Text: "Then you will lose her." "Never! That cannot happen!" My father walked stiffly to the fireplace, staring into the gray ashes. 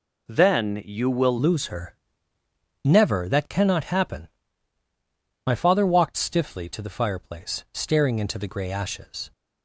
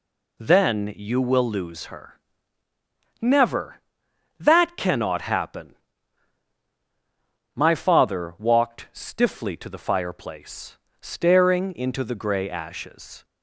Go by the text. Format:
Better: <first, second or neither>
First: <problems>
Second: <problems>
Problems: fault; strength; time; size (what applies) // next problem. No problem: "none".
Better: second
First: changes voice at "lose"; from 1.3 s on; 8.0 s long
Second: none